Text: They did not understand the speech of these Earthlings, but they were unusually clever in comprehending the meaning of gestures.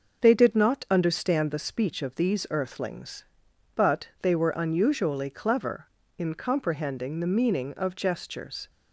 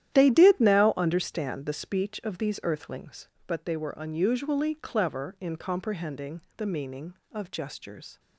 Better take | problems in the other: first | starts louder than the rest; strong; until 1.1 s; 11.5 dB // says "now" for "not"; at 0.5 s // pauses between "comprehending" and "the"; slight; at 6.4 s; 0.16 s long

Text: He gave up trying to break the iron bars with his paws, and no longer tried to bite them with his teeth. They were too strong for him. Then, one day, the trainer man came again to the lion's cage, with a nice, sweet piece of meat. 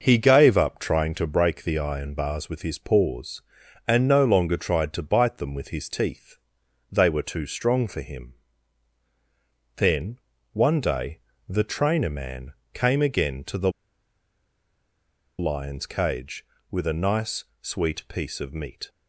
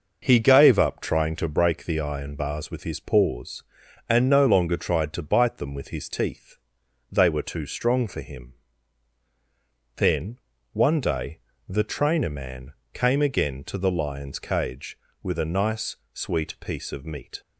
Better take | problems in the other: second | pauses between "man" and "came"; slight; at 12.5 s; 0.20 s long; slight in the second // pauses between "the" and "lion's"; strong; at 13.6 s; 1.6 s long

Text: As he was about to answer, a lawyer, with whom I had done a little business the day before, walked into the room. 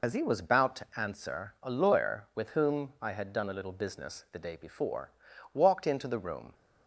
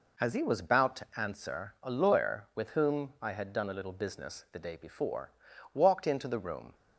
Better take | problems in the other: second | loses the start of "As"; at 0.0 s; 55 ms

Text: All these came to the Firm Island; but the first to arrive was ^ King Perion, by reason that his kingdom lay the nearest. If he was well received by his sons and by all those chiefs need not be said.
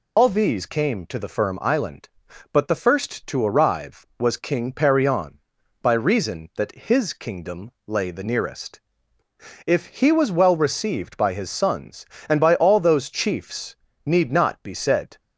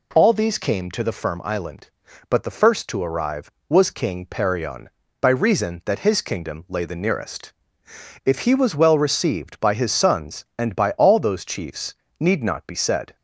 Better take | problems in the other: second | loses the start of "All"; at 0.1 s; 100 ms // pauses between "chiefs" and "need"; slight; at 13.7 s; 0.28 s long; slight in the second

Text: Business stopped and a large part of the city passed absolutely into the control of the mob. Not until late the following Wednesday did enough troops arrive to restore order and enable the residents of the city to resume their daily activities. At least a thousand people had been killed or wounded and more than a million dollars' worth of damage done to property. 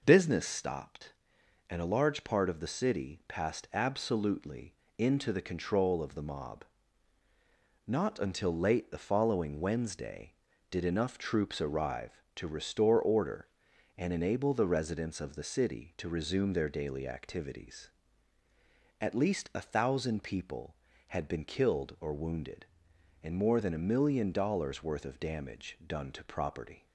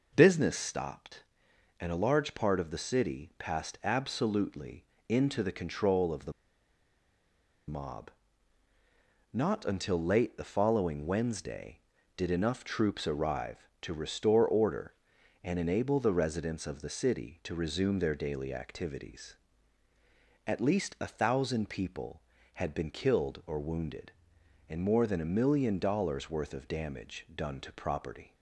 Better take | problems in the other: first | pauses between "absolutely" and "into"; slight; at 4.8 s; 0.24 s long; slight in the first // pauses between "the" and "mob"; strong; at 6.3 s; 1.3 s long

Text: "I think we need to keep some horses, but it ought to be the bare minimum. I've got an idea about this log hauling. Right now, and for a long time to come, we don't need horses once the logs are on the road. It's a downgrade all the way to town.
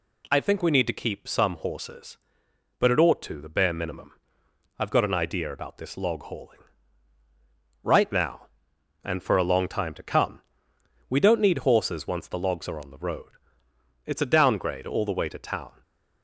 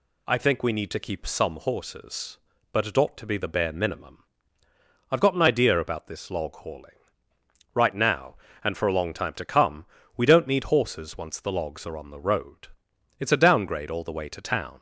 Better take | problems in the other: second | skips "be"; at 3.3 s

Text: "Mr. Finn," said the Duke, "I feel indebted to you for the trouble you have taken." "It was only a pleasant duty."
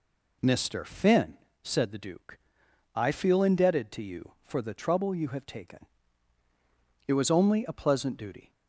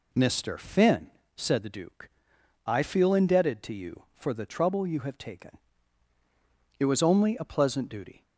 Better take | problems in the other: neither | none

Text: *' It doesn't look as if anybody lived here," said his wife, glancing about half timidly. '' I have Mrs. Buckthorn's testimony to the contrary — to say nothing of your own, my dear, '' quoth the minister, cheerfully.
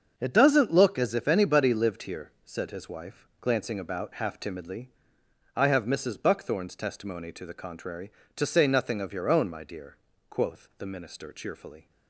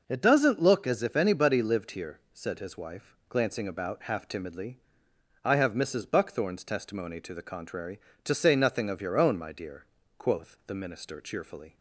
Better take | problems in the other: second | gets quieter; strong; throughout; 10.5 dB

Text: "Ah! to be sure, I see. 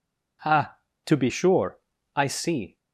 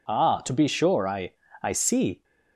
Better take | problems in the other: first | says "I" twice; at 1.6 s

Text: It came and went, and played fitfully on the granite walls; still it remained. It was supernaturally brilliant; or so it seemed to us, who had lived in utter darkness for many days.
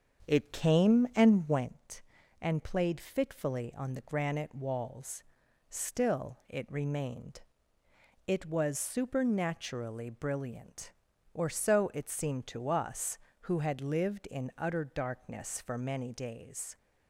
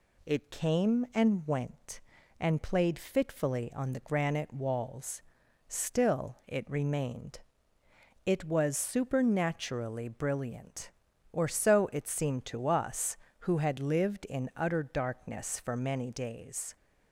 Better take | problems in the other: second | starts louder than the rest; strong; until 1.7 s; 7.5 dB

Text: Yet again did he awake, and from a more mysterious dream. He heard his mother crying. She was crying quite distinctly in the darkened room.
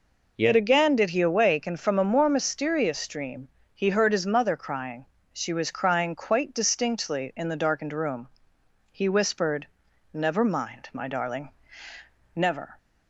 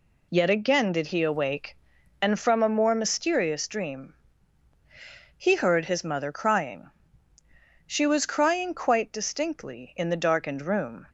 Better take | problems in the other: second | goes on to say "He whispered Never mind my darling never"; strong; from 8.9 s on; 3.8 s long

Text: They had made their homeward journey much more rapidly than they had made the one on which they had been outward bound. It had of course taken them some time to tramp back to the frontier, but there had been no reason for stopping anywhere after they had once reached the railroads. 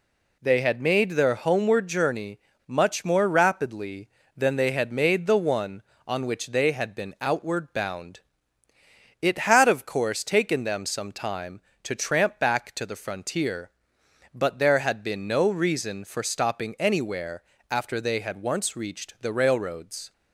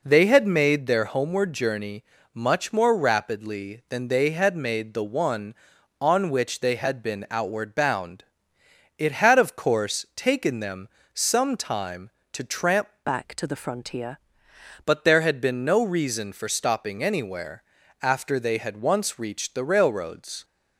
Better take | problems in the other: first | pauses between "journey" and "much"; slight; at 2.0 s; 0.30 s long; slight in the first // pauses between "them" and "some"; slight; at 10.8 s; 0.26 s long // changes voice from "back" to "frontier"; from 13.0 to 14.1 s; 1.1 s long // pauses between "anywhere" and "after"; at 17.6 s; 0.40 s long; slight in the first

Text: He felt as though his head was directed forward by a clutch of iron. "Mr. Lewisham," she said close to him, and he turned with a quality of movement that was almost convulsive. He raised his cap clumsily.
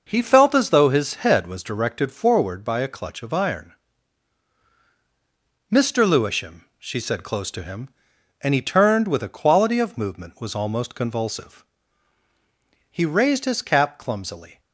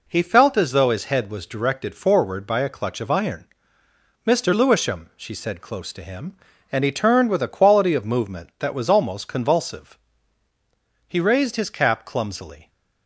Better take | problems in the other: second | skips "that"; at 10.3 s

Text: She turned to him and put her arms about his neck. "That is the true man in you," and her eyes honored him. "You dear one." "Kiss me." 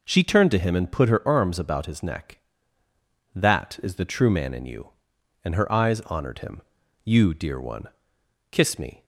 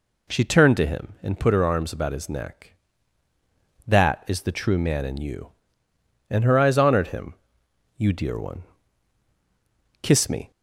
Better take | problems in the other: neither | none

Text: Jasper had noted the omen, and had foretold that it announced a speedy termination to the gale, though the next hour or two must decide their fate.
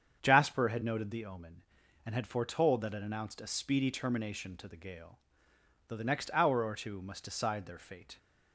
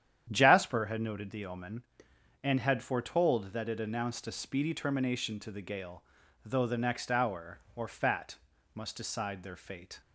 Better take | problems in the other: first | starts louder than the rest; strong; until 1.3 s; 9.5 dB; strong in the first // says "fat" for "two"; at 7.8 s

